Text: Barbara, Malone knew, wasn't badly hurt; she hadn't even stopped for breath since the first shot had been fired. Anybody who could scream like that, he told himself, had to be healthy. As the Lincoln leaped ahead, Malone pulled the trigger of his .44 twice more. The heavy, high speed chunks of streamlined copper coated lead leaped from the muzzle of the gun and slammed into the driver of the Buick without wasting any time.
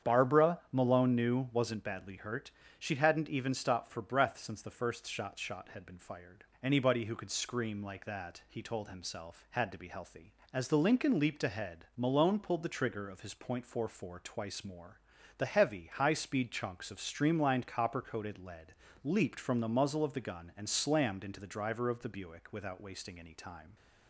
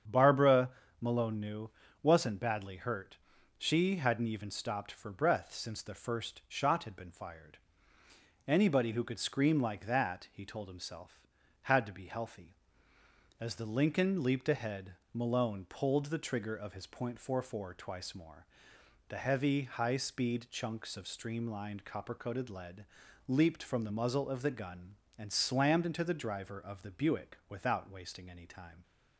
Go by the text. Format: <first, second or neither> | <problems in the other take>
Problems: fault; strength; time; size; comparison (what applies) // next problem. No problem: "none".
second | starts louder than the rest; strong; until 1.1 s; 8 dB; strong in the second // says "shot" twice; at 5.3 s // pauses between "lead" and "leaped"; slight; at 18.7 s; 0.32 s long; also in the second